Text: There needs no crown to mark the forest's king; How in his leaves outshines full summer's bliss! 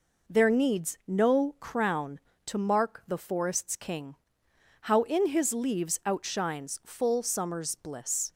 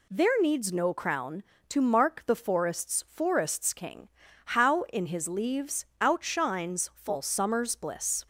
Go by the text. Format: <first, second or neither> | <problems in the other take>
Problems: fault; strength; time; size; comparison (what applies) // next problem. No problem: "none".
first | says "forest's" twice; at 3.0 s // pauses between "leaves" and "outshines"; slight; at 5.8 s; 0.16 s long